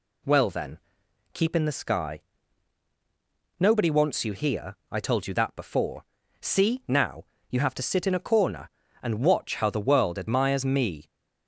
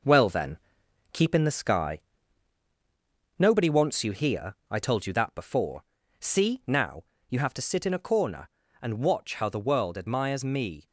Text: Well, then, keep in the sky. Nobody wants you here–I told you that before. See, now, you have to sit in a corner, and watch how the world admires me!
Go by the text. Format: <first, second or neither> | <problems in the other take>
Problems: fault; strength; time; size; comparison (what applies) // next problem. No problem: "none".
first | gets quieter; noticeable; throughout; 5.5 dB